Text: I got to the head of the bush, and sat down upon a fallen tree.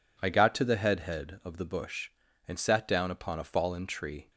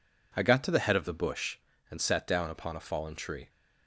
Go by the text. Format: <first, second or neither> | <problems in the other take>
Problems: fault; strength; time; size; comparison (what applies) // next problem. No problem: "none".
second | says "head" twice; at 1.0 s